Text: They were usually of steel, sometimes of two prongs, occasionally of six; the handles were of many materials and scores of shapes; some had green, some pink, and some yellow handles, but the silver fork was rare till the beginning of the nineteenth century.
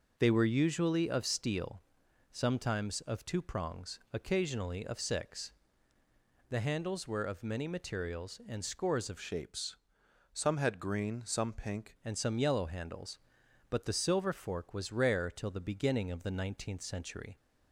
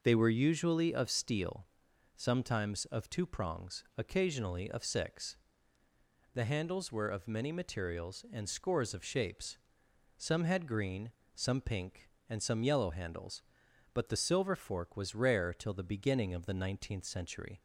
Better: second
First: changes voice from "shapes" to "pink"; from 9.1 to 11.9 s; 2.8 s long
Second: none

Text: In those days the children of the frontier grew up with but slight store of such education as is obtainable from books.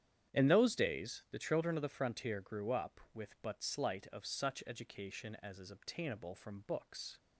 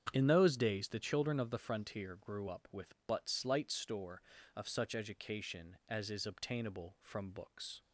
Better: second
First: starts louder than the rest; strong; until 1.4 s; 9.5 dB // skips "store"; at 4.0 s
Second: starts louder than the rest; strong; until 1.1 s; 8 dB

